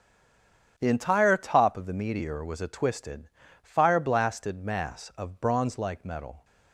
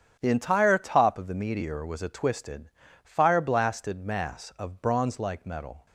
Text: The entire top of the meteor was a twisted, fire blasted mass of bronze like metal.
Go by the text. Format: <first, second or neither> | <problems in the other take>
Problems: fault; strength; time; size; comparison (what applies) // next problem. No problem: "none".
second | stays silent before the first word; slight; until 0.7 s; 0.7 s long // starts louder than the rest; strong; until 1.7 s; 8 dB; strong in the second